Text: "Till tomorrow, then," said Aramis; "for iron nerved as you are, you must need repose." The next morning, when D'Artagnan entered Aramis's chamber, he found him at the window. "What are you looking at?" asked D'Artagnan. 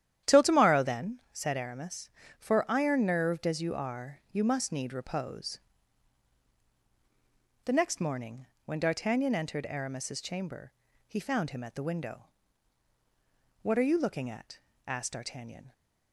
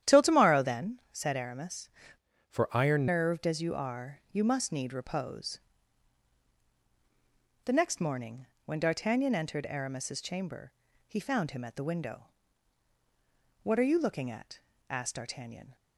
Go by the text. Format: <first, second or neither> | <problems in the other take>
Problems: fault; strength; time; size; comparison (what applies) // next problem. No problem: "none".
first | starts louder than the rest; strong; until 1.1 s; 10.5 dB; strong in the first // changes voice from "for" to "iron"; from 2.4 to 3.0 s; 0.6 s long